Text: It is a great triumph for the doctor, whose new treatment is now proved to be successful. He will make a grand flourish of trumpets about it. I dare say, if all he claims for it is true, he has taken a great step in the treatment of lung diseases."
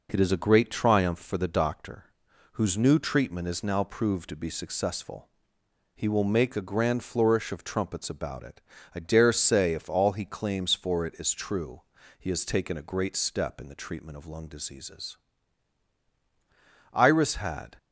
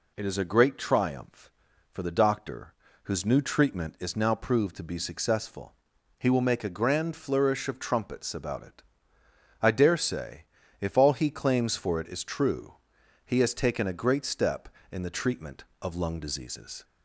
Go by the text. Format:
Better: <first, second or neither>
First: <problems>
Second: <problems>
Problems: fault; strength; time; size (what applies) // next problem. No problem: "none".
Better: second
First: goes on to say "Iris had"; noticeable; from 16.9 s on; 0.84 s long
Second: none